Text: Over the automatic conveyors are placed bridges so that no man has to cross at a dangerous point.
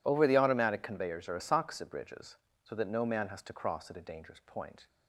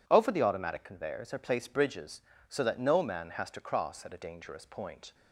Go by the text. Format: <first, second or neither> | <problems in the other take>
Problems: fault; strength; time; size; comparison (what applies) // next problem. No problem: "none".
second | says "asakusa" for "placed"; at 1.3 s